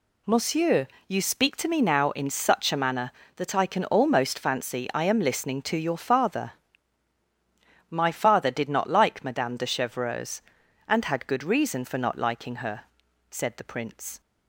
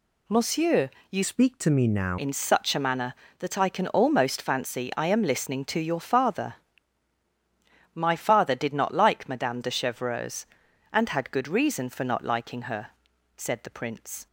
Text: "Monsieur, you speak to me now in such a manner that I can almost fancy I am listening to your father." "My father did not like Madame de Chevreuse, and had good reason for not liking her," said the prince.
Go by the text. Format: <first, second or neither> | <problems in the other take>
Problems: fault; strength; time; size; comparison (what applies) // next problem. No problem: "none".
first | changes voice from "speak" to "now"; from 1.2 to 2.1 s; 0.9 s long